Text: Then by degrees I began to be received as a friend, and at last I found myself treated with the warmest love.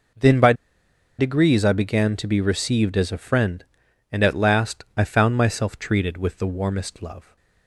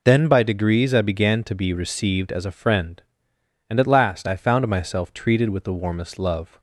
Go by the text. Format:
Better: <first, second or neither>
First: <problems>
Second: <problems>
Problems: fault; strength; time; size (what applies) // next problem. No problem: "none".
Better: second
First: pauses between "by" and "degrees"; noticeable; at 0.5 s; 0.65 s long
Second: none